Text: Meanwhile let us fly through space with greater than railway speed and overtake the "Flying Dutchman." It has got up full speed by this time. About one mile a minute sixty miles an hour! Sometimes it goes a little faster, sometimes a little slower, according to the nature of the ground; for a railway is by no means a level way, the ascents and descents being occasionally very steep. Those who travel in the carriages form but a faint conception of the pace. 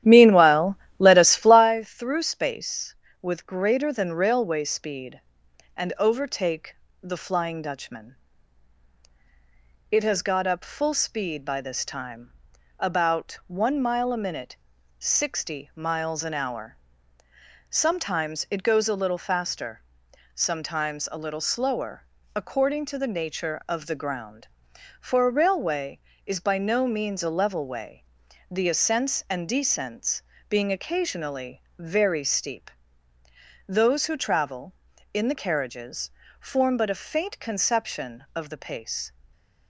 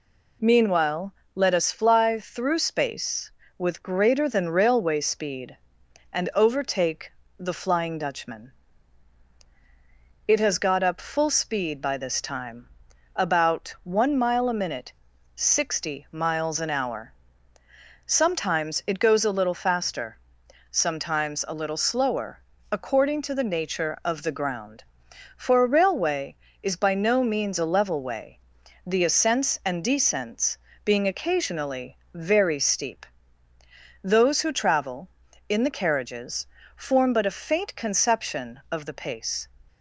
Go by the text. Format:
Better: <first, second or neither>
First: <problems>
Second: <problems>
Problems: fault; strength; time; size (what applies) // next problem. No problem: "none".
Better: second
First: starts louder than the rest; strong; until 1.8 s; 12 dB // pauses between "Meanwhile" and "let"; slight; at 0.7 s; 0.22 s long // pauses between "overtake" and "the"; slight; at 6.7 s; 0.26 s long // pauses between "minute" and "sixty"; at 14.5 s; 0.42 s long // pauses between "descents" and "being"; slight; at 30.2 s; 0.30 s long // pauses between "occasionally" and "very"; slight; at 31.6 s; 0.16 s long // pauses between "carriages" and "form"; slight; at 36.1 s; 0.28 s long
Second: pauses between "Meanwhile" and "let"; slight; at 1.1 s; 0.22 s long // pauses between "overtake" and "the"; slight; at 7.1 s; 0.26 s long // pauses between "minute" and "sixty"; at 14.9 s; 0.42 s long // pauses between "descents" and "being"; slight; at 30.5 s; 0.30 s long // pauses between "occasionally" and "very"; slight; at 31.9 s; 0.16 s long // pauses between "carriages" and "form"; slight; at 36.4 s; 0.28 s long